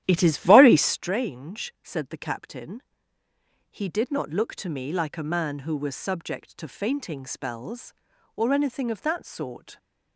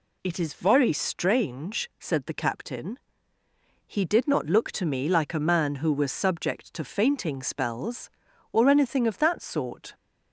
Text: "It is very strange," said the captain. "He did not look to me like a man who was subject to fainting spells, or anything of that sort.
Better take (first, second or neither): second